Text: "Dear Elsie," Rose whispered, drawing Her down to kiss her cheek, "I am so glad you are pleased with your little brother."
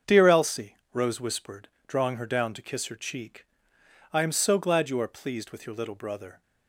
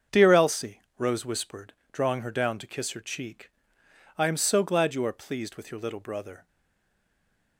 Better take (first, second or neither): first